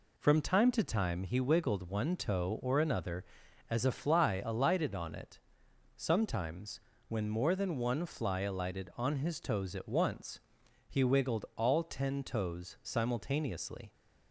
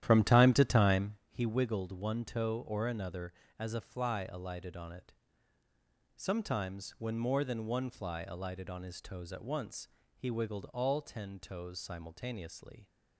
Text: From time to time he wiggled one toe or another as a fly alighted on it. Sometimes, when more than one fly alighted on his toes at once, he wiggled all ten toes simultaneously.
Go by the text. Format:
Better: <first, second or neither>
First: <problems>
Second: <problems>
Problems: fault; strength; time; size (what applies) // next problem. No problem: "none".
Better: first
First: none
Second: starts louder than the rest; strong; until 1.2 s; 11.5 dB // pauses between "time" and "he"; slight; at 1.1 s; 0.16 s long